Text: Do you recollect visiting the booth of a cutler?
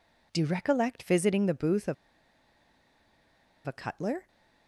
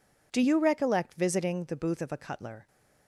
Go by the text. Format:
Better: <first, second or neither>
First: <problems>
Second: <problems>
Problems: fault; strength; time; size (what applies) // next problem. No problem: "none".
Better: second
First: pauses between "of" and "a"; strong; at 1.9 s; 1.7 s long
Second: none